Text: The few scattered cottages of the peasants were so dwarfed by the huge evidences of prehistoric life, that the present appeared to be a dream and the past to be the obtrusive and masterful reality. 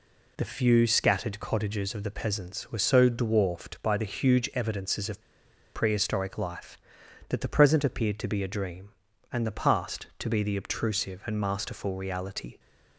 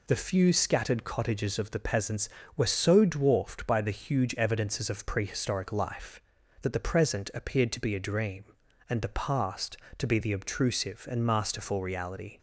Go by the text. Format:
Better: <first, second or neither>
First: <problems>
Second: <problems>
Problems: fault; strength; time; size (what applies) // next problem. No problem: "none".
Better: second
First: pauses between "of" and "prehistoric"; noticeable; at 5.2 s; 0.52 s long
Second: none